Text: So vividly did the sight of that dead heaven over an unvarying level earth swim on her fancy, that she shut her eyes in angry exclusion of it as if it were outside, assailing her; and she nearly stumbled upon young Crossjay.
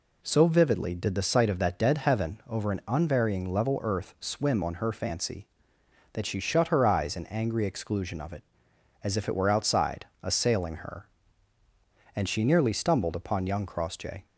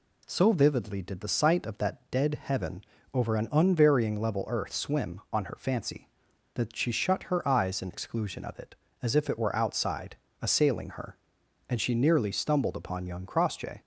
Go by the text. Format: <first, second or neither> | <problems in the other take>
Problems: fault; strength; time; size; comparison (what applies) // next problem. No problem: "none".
first | pauses between "heaven" and "over"; slight; at 2.8 s; 0.30 s long // skips "angry"; at 7.9 s